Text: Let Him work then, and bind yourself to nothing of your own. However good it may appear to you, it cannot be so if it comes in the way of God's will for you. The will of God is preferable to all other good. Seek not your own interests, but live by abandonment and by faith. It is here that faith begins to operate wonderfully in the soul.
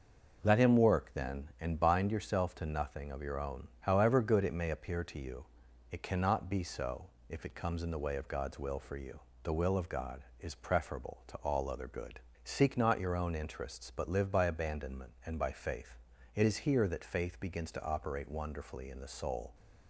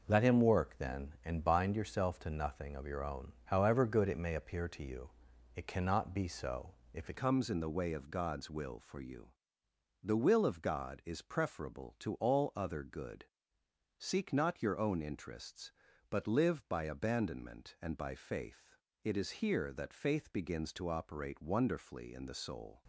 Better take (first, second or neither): first